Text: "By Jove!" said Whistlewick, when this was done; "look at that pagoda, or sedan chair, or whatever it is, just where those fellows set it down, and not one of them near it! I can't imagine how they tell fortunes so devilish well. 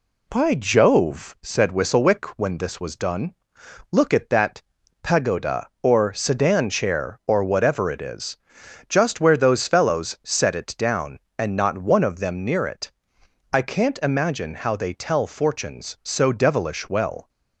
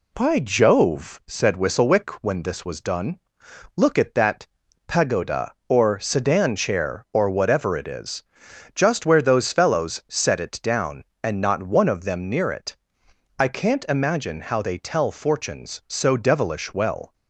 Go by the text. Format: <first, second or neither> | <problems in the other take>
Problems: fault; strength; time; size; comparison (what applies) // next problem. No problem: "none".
neither | pauses between "that" and "pagoda"; the same in both